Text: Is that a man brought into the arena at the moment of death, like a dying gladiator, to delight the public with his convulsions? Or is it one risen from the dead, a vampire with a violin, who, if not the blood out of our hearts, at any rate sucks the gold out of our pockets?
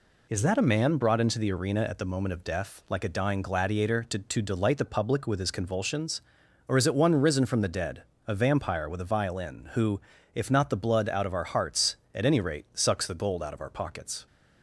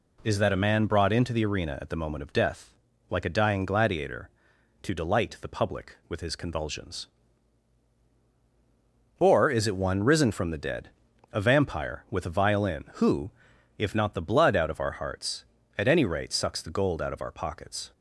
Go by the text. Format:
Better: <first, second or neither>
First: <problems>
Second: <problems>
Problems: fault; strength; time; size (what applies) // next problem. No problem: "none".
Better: second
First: says "to" twice; at 4.1 s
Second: none